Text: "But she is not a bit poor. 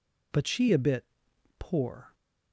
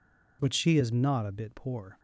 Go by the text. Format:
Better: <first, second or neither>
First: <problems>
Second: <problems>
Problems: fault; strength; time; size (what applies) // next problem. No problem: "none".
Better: second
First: skips "is not"; at 0.6 s // pauses between "bit" and "poor"; noticeable; at 1.0 s; 0.52 s long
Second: none